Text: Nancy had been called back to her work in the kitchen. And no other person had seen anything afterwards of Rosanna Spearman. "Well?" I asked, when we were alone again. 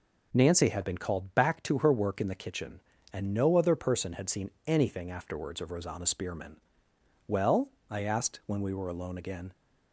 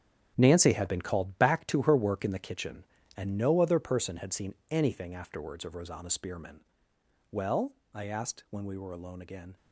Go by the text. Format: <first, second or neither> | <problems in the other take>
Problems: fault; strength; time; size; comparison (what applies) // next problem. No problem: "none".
first | gets quieter; strong; throughout; 11.5 dB